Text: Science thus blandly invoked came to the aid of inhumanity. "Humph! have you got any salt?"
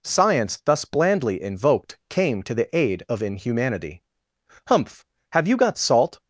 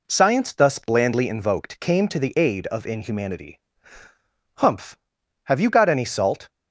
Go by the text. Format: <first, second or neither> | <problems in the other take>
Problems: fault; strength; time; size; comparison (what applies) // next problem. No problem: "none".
second | skips "any"; at 5.7 s